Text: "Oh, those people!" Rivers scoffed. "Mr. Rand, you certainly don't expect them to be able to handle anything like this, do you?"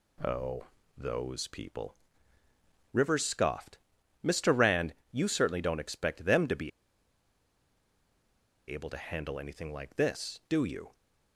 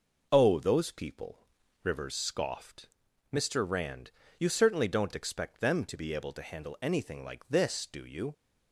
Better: second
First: pauses between "be" and "able"; strong; at 6.7 s; 1.9 s long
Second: none

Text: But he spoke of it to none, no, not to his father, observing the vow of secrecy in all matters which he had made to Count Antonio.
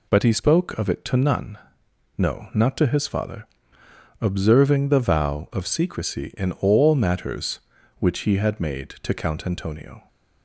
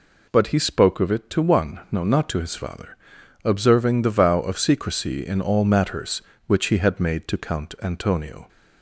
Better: first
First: none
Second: says "one" for "none"; at 1.4 s

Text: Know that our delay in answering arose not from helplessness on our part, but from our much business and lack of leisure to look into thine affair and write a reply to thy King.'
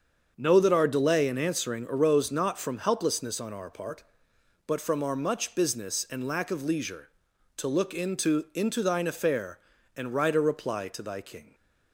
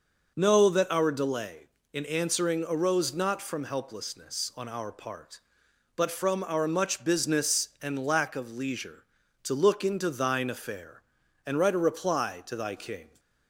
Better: second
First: starts louder than the rest; until 1.3 s; 7 dB // says "into" twice; at 8.5 s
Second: none

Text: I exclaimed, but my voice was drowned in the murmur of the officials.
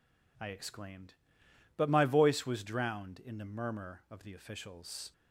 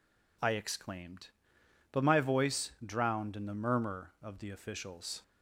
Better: first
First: none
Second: skips "was"; at 2.7 s

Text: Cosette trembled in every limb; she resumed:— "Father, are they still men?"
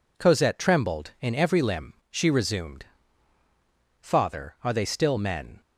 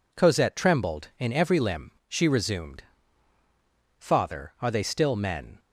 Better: neither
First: none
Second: none

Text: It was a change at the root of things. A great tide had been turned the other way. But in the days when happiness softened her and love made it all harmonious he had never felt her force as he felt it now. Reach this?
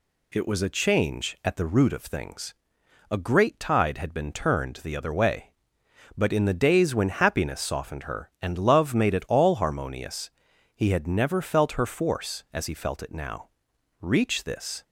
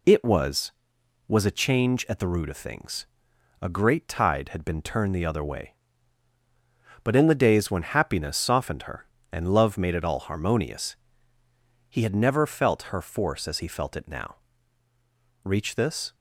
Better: first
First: pauses between "harmonious" and "he"; at 10.3 s; 0.44 s long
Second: says "was" twice; at 1.2 s // pauses between "harmonious" and "he"; noticeable; at 10.9 s; 0.92 s long

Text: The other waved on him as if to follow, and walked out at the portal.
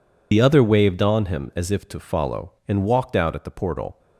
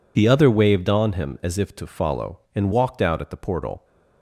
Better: second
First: loses the start of "The"; at 0.3 s; 30 ms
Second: none

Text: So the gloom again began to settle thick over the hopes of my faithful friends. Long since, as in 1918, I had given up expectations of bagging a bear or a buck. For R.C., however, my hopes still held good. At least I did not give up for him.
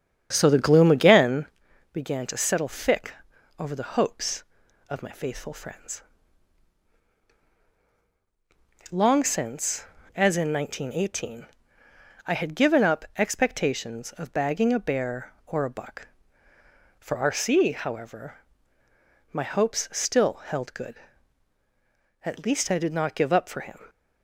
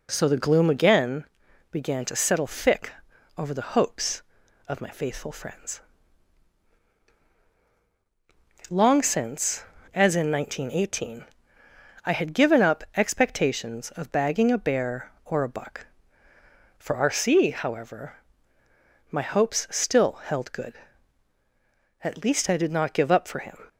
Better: second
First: starts louder than the rest; strong; until 1.7 s; 8 dB // pauses between "again" and "began"; noticeable; at 1.4 s; 0.46 s long // pauses between "thick" and "over"; noticeable; at 3.1 s; 0.48 s long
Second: pauses between "again" and "began"; noticeable; at 1.2 s; 0.46 s long // pauses between "thick" and "over"; noticeable; at 2.8 s; 0.48 s long

